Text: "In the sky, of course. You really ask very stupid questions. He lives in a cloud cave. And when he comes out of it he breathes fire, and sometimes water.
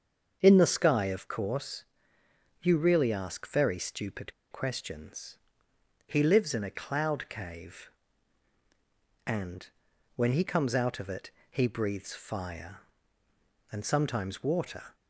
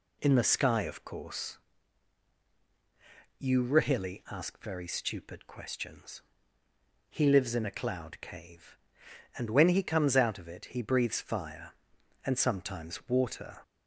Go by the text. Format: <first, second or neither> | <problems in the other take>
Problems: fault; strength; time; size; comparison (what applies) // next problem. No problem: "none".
second | starts louder than the rest; until 1.4 s; 7 dB // pauses between "stupid" and "questions"; slight; at 4.3 s; 0.19 s long // pauses between "And" and "when"; noticeable; at 9.6 s; 0.48 s long // pauses between "it" and "he"; slight; at 11.3 s; 0.20 s long